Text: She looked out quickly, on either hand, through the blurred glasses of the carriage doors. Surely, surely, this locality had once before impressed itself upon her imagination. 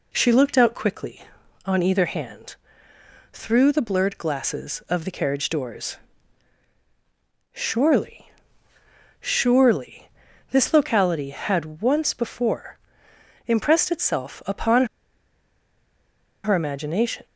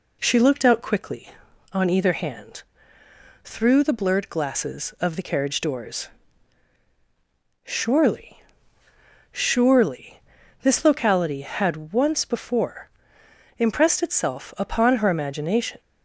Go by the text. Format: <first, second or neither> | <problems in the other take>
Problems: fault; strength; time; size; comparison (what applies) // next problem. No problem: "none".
second | pauses between "before" and "impressed"; noticeable; at 12.7 s; 0.70 s long; noticeable in the second // pauses between "upon" and "her"; strong; at 14.8 s; 1.5 s long